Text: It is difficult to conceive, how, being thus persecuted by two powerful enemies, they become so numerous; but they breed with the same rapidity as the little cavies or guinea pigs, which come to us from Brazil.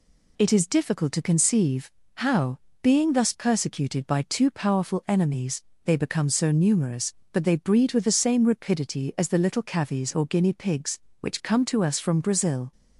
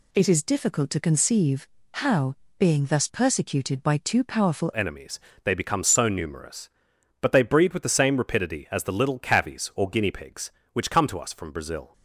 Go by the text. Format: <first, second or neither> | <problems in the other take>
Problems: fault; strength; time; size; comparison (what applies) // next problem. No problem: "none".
first | changes voice at "enemies"; from 4.7 s on; 7.2 s long